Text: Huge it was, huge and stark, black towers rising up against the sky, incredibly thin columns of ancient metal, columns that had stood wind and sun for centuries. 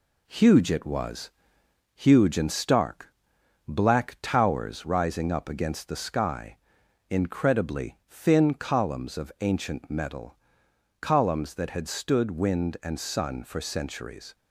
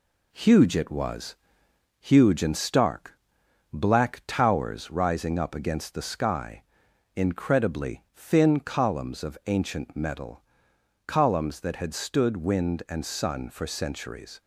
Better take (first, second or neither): neither